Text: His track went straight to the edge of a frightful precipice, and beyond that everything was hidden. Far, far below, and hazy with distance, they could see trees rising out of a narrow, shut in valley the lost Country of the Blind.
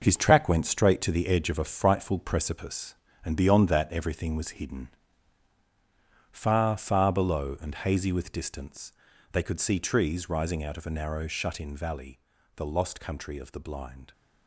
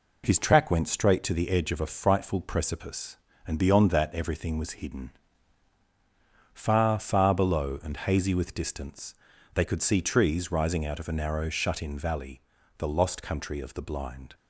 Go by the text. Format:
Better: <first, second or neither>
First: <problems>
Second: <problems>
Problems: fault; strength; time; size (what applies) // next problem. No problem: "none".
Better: second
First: gets quieter; strong; throughout; 8.5 dB // pauses between "valley" and "the"; at 12.1 s; 0.38 s long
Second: pauses between "valley" and "the"; at 12.4 s; 0.38 s long